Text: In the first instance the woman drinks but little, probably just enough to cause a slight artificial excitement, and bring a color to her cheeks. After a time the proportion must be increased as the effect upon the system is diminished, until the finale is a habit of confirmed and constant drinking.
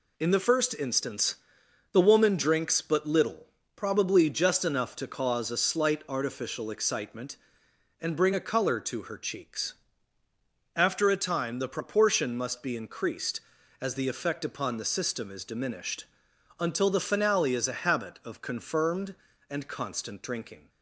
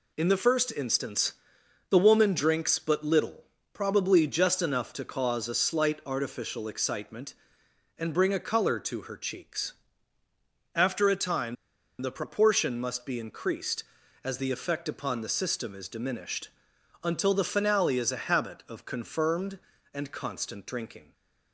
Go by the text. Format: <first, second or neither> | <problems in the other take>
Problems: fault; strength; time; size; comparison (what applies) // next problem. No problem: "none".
first | pauses between "instance" and "the"; noticeable; at 1.3 s; 0.56 s long; noticeable in the first // pauses between "time" and "the"; at 11.5 s; 0.45 s long